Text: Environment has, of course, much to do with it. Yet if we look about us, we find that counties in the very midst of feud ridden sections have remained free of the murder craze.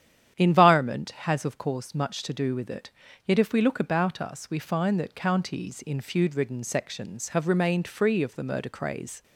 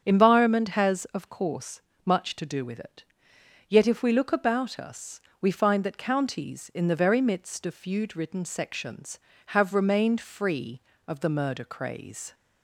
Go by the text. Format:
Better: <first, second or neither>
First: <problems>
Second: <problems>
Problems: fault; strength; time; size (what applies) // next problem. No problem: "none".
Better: second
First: starts louder than the rest; strong; until 1.3 s; 9.5 dB // skips "the very midst of"; at 6.0 s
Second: starts louder than the rest; strong; until 1.0 s; 8 dB